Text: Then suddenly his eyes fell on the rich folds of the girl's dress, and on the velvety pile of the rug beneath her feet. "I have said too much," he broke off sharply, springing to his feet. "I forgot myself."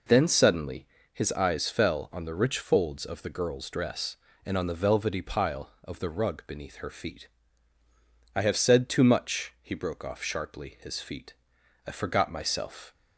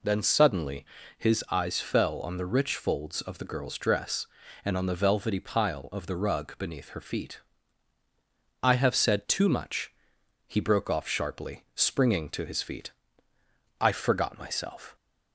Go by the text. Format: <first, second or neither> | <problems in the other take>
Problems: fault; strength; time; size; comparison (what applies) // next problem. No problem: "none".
second | pauses between "suddenly" and "his"; slight; at 0.8 s; 0.26 s long; slight in the second // skips "springing to"; at 10.7 s